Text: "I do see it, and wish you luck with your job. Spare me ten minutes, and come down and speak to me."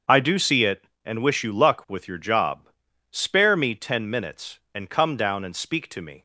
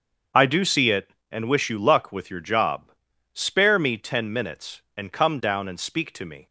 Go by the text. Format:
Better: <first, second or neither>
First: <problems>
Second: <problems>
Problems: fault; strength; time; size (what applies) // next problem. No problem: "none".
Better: neither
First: starts louder than the rest; until 1.2 s; 7 dB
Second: starts louder than the rest; until 1.5 s; 7 dB